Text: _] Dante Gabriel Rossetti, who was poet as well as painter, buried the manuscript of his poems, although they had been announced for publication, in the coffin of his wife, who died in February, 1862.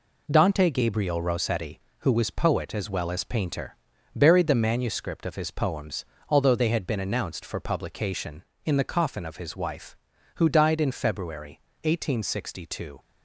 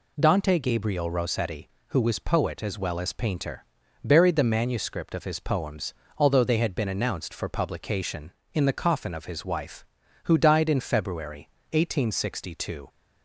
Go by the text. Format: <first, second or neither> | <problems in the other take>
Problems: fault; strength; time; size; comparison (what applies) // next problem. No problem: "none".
second | gets quieter; noticeable; throughout; 6 dB